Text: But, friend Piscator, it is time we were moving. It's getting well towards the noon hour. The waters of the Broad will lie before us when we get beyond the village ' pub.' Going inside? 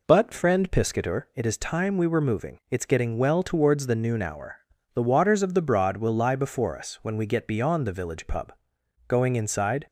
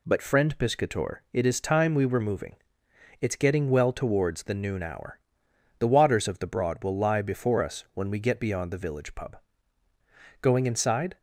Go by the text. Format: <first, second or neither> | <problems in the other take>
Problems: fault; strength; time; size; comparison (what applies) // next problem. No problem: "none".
neither | none